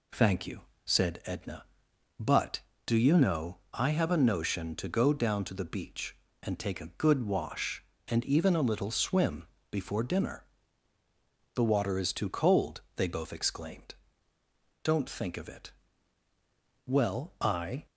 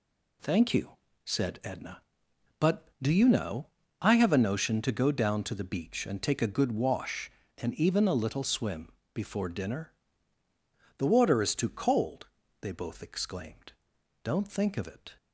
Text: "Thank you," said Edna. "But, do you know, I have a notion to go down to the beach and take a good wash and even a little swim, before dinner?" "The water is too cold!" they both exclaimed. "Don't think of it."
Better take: second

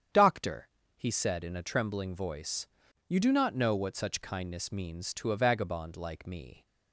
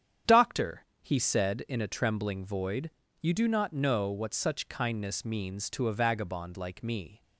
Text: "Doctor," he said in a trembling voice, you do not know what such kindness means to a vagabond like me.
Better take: first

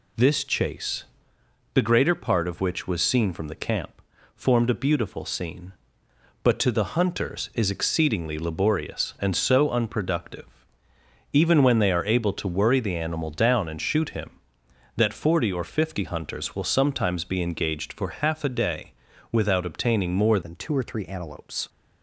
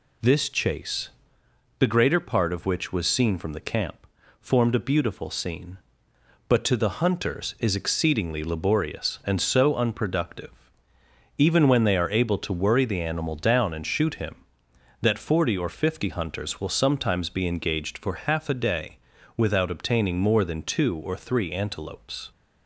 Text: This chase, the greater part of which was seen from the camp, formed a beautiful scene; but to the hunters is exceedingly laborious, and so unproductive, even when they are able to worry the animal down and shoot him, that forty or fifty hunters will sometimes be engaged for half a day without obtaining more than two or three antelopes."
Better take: second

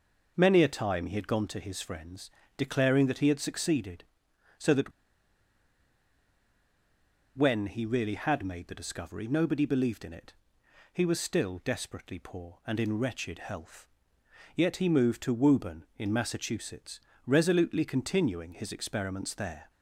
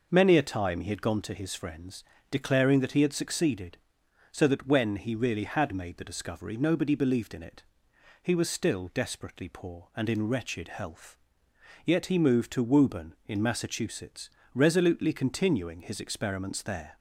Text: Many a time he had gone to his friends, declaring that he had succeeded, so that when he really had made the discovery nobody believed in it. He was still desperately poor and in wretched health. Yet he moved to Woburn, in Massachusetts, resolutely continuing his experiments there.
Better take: second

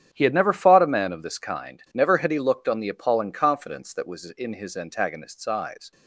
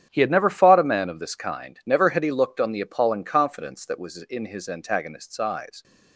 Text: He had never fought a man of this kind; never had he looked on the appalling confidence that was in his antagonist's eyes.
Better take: neither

